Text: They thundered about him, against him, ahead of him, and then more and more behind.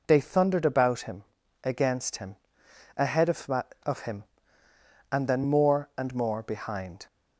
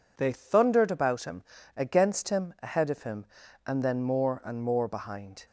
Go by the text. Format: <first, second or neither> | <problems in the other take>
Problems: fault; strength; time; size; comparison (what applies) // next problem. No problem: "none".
second | says "of" twice; at 3.8 s